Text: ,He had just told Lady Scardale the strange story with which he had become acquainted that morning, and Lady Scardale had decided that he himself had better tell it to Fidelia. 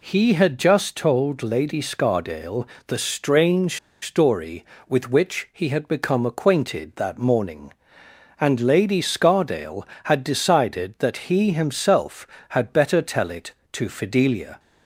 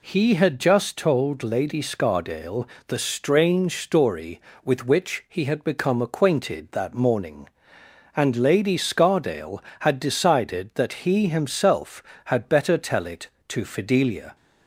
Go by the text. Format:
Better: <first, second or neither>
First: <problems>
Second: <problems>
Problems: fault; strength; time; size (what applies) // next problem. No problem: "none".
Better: second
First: pauses between "Scardale" and "the"; slight; at 2.6 s; 0.22 s long // pauses between "strange" and "story"; slight; at 3.7 s; 0.25 s long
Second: pauses between "Scardale" and "the"; slight; at 2.6 s; 0.22 s long